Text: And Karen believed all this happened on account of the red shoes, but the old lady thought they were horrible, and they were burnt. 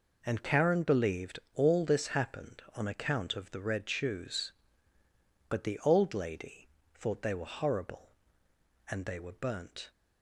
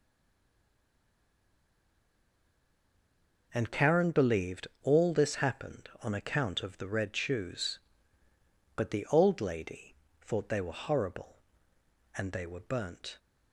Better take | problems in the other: first | stays silent before the first word; strong; until 3.5 s; 3.5 s long // pauses between "believed" and "all"; slight; at 4.6 s; 0.16 s long; slight in the first // pauses between "lady" and "thought"; slight; at 9.9 s; 0.26 s long; slight in the first

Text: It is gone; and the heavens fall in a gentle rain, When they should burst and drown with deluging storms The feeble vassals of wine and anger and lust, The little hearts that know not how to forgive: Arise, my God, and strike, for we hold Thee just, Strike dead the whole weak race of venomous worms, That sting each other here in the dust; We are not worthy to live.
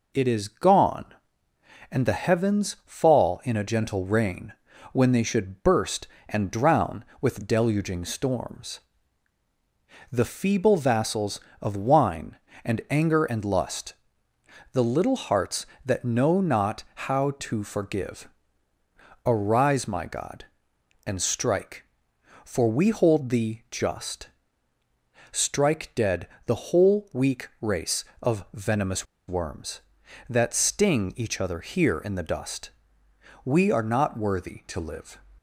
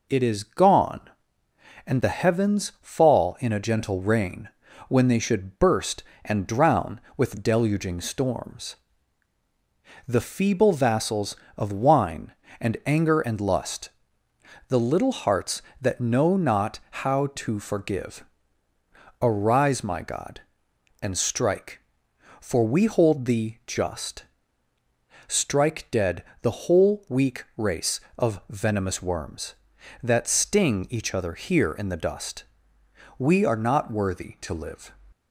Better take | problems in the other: second | pauses between "storms" and "The"; strong; at 8.8 s; 1.3 s long; strong in the second // pauses between "dead" and "the"; slight; at 26.2 s; 0.18 s long; slight in the second // pauses between "venomous" and "worms"; slight; at 29.0 s; 0.23 s long

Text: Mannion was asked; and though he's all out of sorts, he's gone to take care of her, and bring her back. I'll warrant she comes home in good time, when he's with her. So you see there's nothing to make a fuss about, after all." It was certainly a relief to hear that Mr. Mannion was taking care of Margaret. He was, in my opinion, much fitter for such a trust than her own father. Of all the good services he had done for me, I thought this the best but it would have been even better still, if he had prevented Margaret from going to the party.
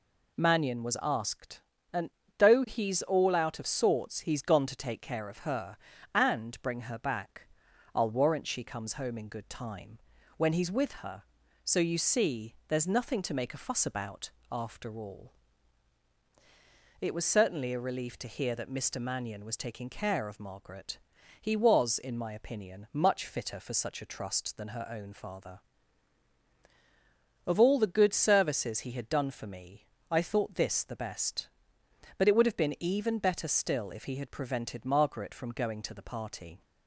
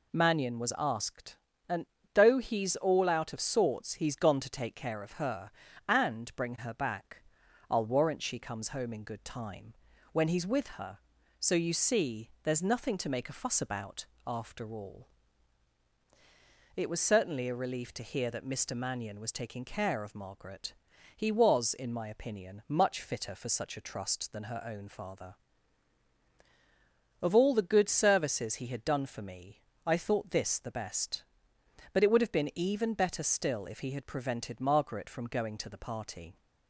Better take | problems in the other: neither | pauses between "and" and "though"; slight; the same in both

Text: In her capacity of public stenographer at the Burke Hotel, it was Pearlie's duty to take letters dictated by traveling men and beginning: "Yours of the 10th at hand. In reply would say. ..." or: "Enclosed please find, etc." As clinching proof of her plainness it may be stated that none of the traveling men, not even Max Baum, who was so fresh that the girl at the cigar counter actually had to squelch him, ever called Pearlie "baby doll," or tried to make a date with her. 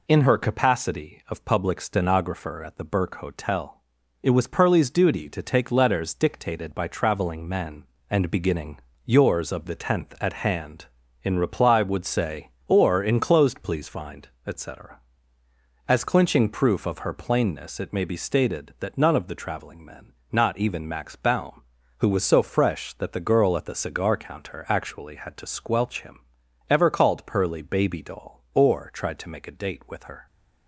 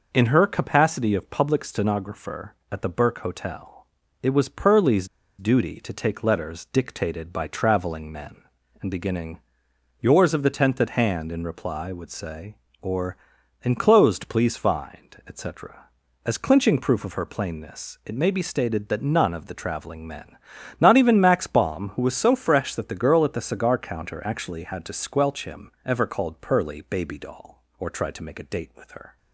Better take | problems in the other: first | pauses between "Pearlie's" and "duty"; slight; at 5.0 s; 0.32 s long

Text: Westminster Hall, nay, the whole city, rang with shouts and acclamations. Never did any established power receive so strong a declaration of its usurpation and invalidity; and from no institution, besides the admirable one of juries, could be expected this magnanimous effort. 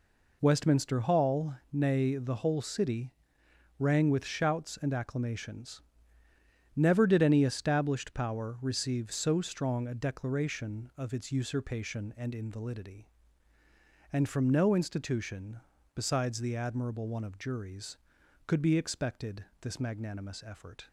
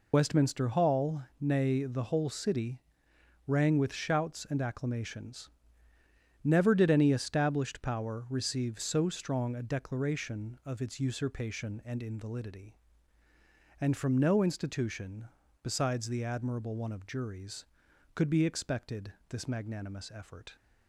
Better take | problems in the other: first | loses the start of "Westminster"; at 0.1 s; 45 ms // pauses between "expected" and "this"; slight; at 19.1 s; 0.16 s long; slight in the first

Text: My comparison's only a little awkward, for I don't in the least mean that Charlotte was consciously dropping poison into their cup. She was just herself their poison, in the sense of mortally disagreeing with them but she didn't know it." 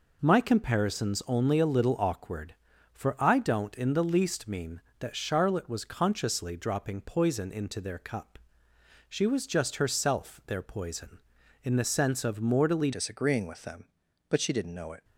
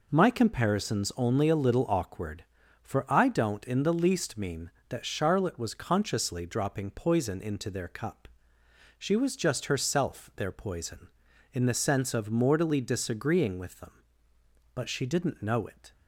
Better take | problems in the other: second | changes voice at "disagreeing"; from 12.9 s on; 2.1 s long

